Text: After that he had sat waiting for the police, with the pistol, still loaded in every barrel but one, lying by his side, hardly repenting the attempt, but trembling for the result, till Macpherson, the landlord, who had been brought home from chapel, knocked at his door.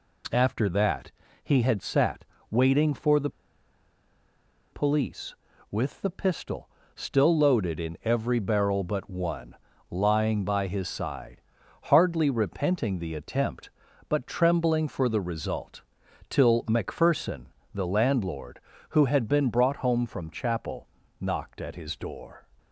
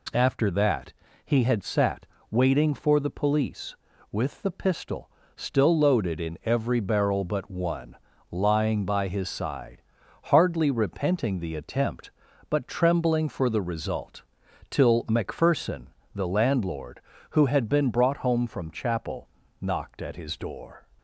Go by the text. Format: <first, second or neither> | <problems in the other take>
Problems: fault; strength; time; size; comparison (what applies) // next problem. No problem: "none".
second | pauses between "that" and "he"; slight; at 1.1 s; 0.32 s long; slight in the second // pauses between "sat" and "waiting"; slight; at 2.2 s; 0.26 s long; slight in the second // pauses between "the" and "police"; strong; at 3.2 s; 1.4 s long